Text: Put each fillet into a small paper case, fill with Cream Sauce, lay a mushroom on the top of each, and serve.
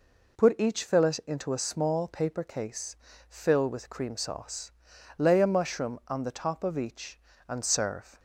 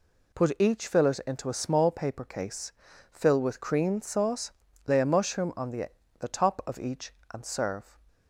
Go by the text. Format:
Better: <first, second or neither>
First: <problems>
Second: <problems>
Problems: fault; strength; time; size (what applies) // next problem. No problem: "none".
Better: first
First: none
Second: says "the" twice; at 6.2 s